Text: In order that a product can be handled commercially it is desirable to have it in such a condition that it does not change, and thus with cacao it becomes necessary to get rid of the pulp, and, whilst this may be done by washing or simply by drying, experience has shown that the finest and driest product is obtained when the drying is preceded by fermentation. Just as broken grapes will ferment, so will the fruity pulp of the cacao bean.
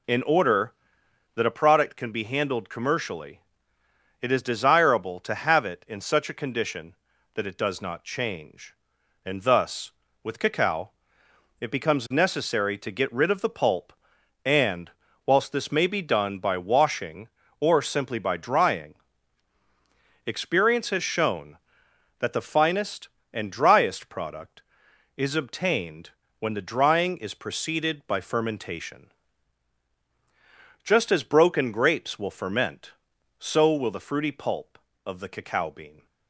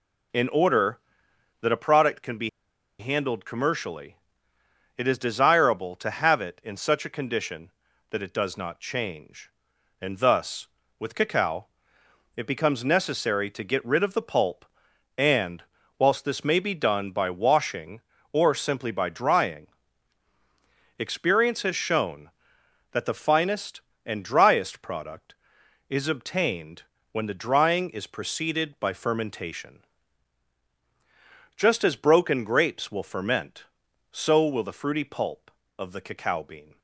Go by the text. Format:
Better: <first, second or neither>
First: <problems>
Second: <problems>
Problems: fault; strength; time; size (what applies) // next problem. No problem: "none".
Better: first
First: pauses between "commercially" and "it"; noticeable; at 3.4 s; 0.80 s long // pauses between "cacao" and "it"; noticeable; at 10.9 s; 0.70 s long // pauses between "obtained" and "when"; slight; at 26.0 s; 0.30 s long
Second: pauses between "be" and "handled"; noticeable; at 2.4 s; 0.50 s long // pauses between "commercially" and "it"; noticeable; at 4.1 s; 0.80 s long // pauses between "cacao" and "it"; noticeable; at 11.6 s; 0.70 s long // pauses between "obtained" and "when"; slight; at 26.8 s; 0.30 s long